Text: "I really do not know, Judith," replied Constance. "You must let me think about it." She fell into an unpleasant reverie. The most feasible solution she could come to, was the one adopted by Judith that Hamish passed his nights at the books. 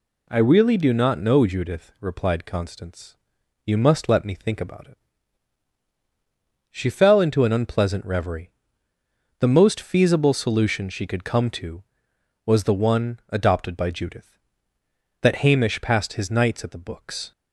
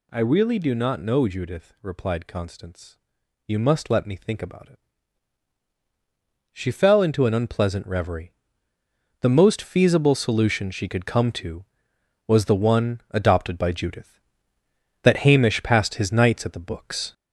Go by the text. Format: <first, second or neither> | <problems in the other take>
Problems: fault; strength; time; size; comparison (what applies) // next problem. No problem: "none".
first | gets louder; noticeable; throughout; 4.5 dB